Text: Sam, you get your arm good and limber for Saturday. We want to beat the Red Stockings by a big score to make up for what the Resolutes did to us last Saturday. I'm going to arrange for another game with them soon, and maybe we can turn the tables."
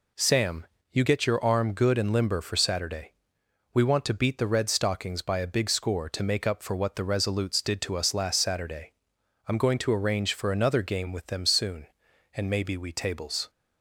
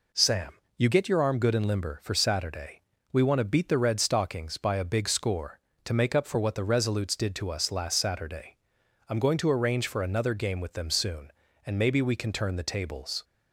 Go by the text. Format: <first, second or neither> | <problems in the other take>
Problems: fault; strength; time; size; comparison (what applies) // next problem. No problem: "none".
second | skips "can turn the"; at 12.9 s